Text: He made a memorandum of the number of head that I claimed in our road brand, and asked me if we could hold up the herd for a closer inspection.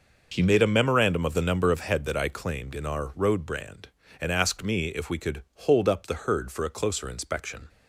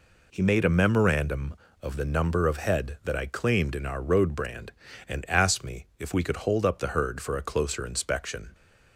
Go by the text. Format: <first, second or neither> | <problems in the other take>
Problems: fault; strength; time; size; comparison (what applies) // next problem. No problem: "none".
neither | none